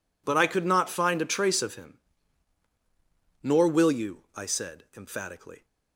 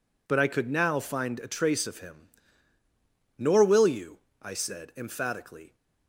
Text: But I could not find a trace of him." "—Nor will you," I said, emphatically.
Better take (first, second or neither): first